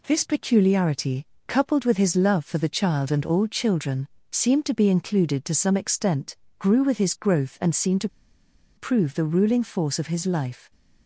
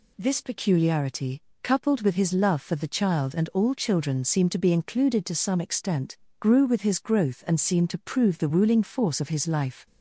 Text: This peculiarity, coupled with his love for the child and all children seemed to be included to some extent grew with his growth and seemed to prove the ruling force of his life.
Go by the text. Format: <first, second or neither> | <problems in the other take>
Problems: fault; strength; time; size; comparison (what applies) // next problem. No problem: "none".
second | pauses between "children" and "seemed"; slight; at 4.0 s; 0.24 s long // pauses between "extent" and "grew"; slight; at 6.3 s; 0.22 s long; slight in the second // pauses between "to" and "prove"; noticeable; at 8.0 s; 0.69 s long